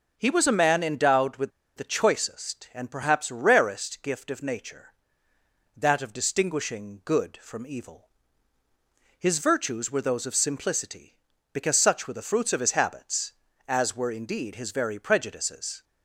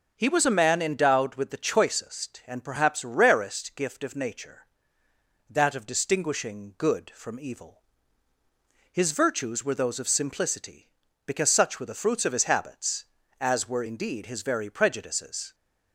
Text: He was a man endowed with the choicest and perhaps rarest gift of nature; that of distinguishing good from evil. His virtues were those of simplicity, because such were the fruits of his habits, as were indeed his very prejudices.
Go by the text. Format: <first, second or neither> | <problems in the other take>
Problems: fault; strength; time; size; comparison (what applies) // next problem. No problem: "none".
second | pauses between "with" and "the"; slight; at 1.5 s; 0.26 s long